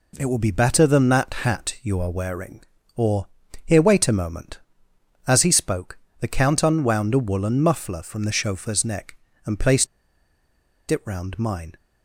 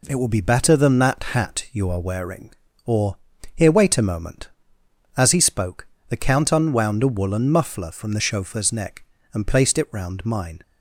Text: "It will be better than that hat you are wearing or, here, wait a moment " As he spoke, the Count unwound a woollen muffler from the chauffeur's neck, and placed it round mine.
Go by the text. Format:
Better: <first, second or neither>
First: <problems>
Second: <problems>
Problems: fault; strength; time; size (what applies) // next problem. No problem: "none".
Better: second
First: pauses between "placed" and "it"; at 9.8 s; 1.0 s long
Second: none